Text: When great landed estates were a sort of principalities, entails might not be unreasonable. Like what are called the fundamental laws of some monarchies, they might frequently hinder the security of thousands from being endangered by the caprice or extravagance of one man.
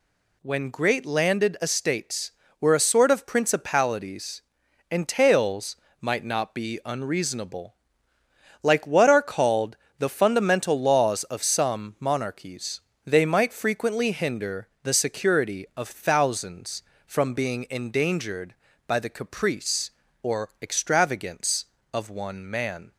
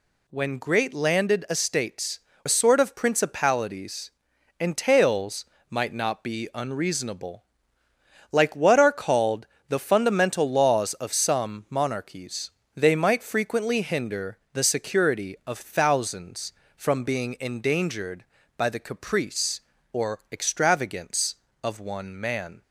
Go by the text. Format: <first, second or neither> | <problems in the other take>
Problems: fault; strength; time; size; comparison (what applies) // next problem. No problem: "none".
first | skips "were"; at 2.3 s // pauses between "entails" and "might"; slight; at 5.4 s; 0.24 s long; slight in the first // pauses between "called" and "the"; slight; at 9.4 s; 0.22 s long; slight in the first // pauses between "hinder" and "the"; slight; at 14.3 s; 0.16 s long; slight in the first